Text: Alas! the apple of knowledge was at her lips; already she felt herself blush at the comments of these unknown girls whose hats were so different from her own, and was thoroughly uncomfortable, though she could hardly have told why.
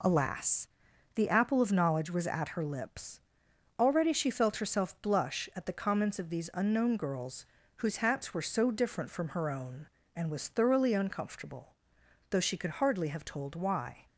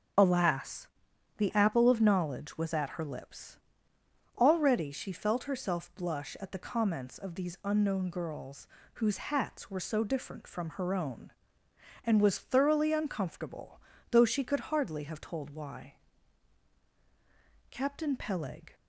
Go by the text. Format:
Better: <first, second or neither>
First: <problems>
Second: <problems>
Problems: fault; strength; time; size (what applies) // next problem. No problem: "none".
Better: first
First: pauses between "girls" and "whose"; slight; at 7.4 s; 0.30 s long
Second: starts louder than the rest; until 1.6 s; 6.5 dB // pauses between "girls" and "whose"; slight; at 8.6 s; 0.28 s long // goes on to say "Captain Peleg"; noticeable; from 17.7 s on; 1.0 s long